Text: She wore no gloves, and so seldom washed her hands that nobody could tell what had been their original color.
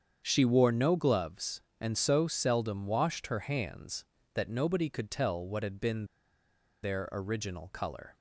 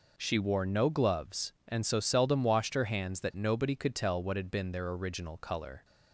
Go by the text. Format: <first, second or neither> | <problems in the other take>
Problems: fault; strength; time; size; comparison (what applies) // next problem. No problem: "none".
second | starts louder than the rest; strong; until 1.2 s; 7.5 dB // pauses between "been" and "their"; noticeable; at 6.0 s; 0.78 s long